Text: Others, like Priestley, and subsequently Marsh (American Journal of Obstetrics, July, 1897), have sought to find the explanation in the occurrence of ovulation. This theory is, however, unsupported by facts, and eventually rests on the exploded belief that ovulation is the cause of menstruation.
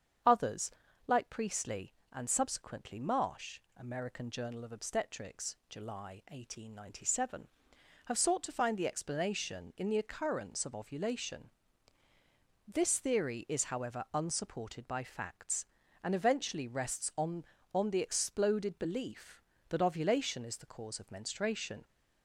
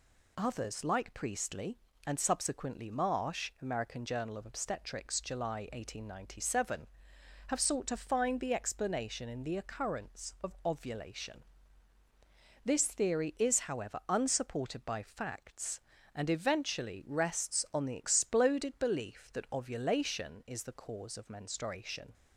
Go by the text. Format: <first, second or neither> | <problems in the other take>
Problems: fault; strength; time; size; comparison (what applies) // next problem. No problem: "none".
second | starts louder than the rest; strong; until 1.6 s; 7.5 dB // says "on" twice; at 17.7 s